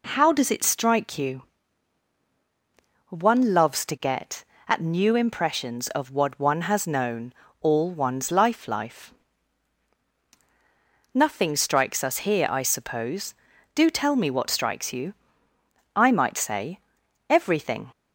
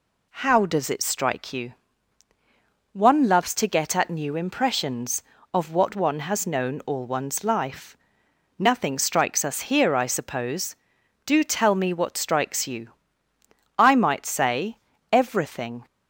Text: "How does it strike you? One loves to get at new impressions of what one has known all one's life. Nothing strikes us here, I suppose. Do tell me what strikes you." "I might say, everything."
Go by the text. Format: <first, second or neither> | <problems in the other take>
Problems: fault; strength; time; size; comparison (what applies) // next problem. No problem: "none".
second | pauses between "known" and "all"; slight; at 7.3 s; 0.28 s long // says "life" twice; at 8.6 s